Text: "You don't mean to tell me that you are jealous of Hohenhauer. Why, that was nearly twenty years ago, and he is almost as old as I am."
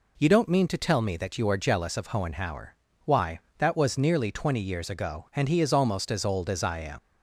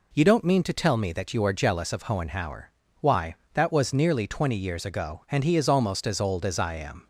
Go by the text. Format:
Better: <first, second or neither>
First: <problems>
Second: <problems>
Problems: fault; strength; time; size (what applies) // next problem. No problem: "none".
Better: second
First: leaves "am" unfinished; at 6.9 s; 125 ms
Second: none